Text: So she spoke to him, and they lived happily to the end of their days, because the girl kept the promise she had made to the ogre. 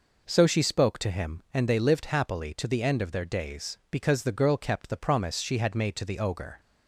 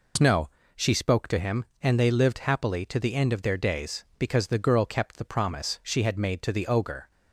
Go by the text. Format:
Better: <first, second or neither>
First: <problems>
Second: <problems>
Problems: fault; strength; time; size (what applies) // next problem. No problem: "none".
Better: first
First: none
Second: says "No" for "So"; at 0.1 s